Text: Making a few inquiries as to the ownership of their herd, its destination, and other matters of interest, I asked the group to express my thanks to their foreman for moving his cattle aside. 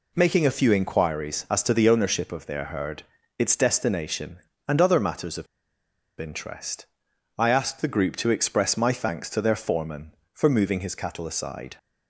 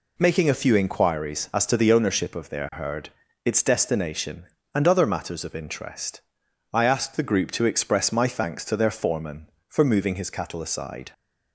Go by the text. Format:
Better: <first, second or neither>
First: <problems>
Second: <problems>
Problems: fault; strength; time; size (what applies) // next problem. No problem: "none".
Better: second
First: pauses between "of" and "interest"; noticeable; at 5.4 s; 0.74 s long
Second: none